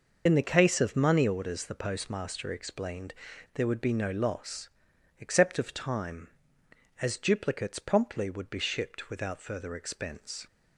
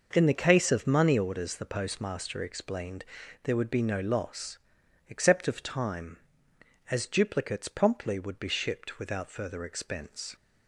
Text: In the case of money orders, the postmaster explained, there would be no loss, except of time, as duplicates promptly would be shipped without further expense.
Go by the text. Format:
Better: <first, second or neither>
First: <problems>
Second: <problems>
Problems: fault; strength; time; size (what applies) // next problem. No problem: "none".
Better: second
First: loses the start of "In"; at 0.2 s; 60 ms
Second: none